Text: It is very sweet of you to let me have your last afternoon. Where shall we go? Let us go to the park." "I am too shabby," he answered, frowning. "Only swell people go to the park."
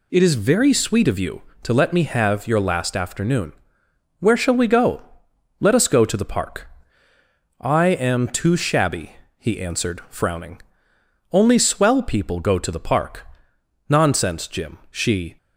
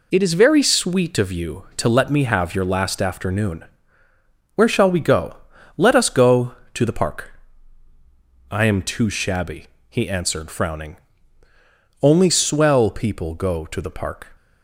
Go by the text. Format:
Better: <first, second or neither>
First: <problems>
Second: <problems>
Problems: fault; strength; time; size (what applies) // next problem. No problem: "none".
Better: second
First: goes on to say "Nonsense Jim she"; from 13.8 s on; 1.4 s long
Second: none